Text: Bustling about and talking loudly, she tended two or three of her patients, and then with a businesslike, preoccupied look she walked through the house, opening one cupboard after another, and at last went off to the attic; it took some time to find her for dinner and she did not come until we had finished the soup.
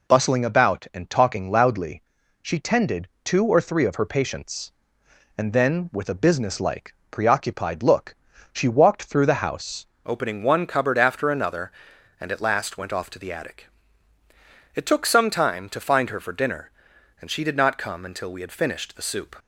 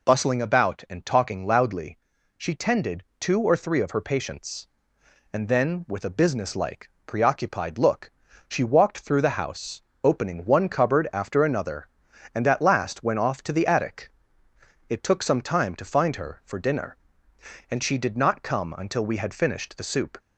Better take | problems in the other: second | pauses between "tended" and "two"; slight; at 3.0 s; 0.16 s long; slight in the second // pauses between "look" and "she"; at 8.1 s; 0.38 s long; also in the second // changes voice at "opening"; from 10.0 s on; 9.3 s long

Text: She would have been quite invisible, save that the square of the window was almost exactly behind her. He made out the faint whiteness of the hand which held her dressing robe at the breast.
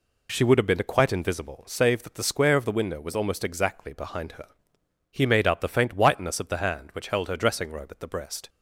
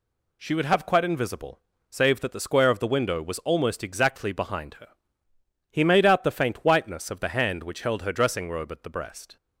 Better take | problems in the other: first | skips "been"; at 0.8 s

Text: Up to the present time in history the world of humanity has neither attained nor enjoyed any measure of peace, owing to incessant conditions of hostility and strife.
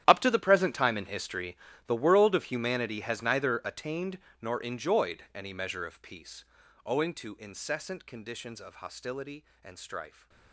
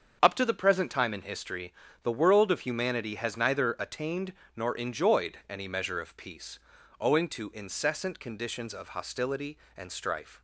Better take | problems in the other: second | gets quieter; strong; throughout; 17.5 dB // starts louder than the rest; strong; until 1.0 s; 11.5 dB; strong in the second // pauses between "history" and "the"; slight; at 1.5 s; 0.32 s long; slight in the second // pauses between "attained" and "nor"; slight; at 4.1 s; 0.22 s long; slight in the second

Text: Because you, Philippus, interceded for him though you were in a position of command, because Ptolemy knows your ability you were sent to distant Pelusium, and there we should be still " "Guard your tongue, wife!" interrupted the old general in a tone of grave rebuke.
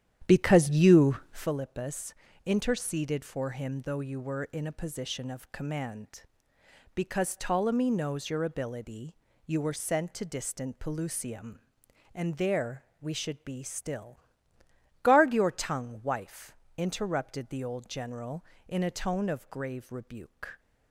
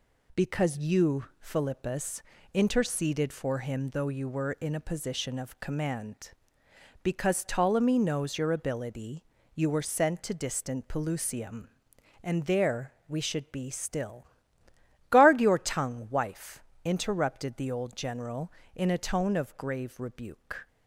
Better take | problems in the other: second | starts louder than the rest; strong; until 1.5 s; 10.5 dB // pauses between "ability" and "you"; slight; at 9.1 s; 0.31 s long; slight in the second // pauses between "there" and "we"; slight; at 12.8 s; 0.16 s long

